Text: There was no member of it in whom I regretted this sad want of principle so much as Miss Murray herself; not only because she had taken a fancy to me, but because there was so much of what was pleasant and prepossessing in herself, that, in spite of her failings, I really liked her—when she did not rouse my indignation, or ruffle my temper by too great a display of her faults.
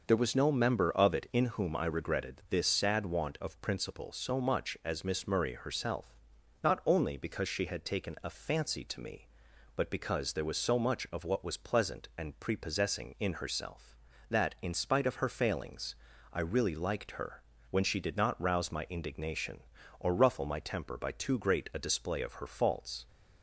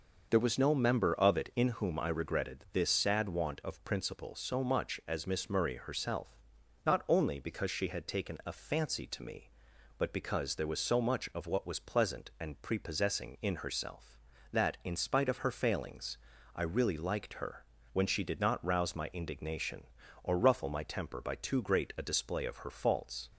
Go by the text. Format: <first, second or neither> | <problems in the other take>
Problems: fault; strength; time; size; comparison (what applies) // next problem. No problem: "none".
neither | none